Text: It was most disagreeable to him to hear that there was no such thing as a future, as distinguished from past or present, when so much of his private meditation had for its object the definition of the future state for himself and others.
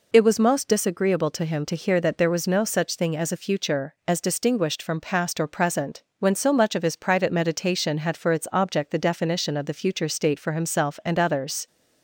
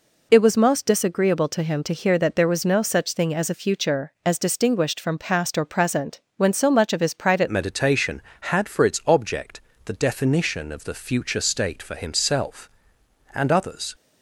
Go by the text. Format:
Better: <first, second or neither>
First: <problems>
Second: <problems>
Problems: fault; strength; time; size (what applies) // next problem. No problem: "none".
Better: first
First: none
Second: changes voice at "meditation"; from 7.4 s on; 6.5 s long // pauses between "object" and "the"; slight; at 9.6 s; 0.24 s long